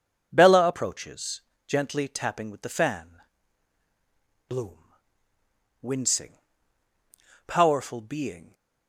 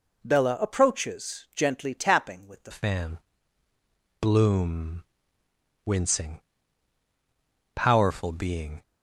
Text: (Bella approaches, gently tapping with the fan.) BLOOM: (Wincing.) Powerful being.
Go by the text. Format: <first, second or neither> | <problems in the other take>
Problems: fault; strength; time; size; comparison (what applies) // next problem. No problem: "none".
first | changes voice at "fan"; from 2.7 s on; 6.1 s long